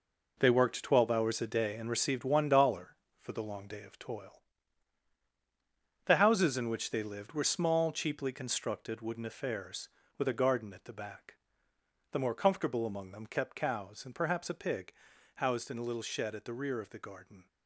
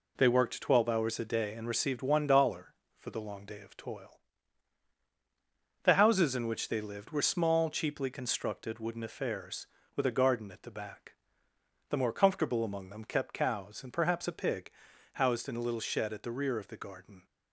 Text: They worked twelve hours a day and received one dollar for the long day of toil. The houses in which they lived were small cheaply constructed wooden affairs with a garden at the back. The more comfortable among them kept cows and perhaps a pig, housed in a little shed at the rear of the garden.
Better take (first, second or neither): second